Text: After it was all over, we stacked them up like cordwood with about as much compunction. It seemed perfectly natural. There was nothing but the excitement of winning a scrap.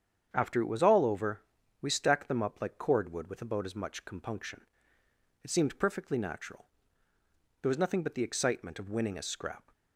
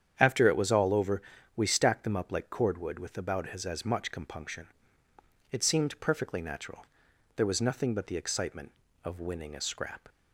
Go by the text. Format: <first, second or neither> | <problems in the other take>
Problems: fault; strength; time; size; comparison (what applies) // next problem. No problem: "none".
first | starts louder than the rest; strong; until 1.1 s; 8.5 dB; strong in the first // says "as" twice; at 3.6 s